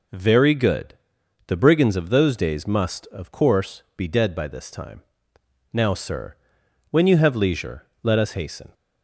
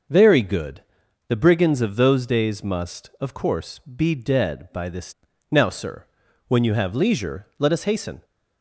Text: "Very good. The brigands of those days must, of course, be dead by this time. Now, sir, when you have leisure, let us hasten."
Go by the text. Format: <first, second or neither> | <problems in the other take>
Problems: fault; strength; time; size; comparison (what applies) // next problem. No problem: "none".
first | starts louder than the rest; until 1.5 s; 6 dB // skips "time"; at 5.3 s